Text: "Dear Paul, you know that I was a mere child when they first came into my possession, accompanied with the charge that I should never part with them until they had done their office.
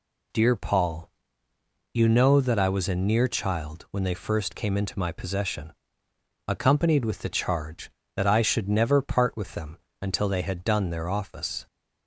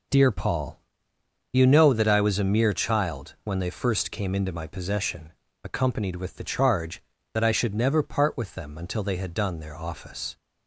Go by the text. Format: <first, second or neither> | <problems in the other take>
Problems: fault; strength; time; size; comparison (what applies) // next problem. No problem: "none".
second | says "near" for "mere"; at 2.9 s // pauses between "them" and "until"; slight; at 9.7 s; 0.22 s long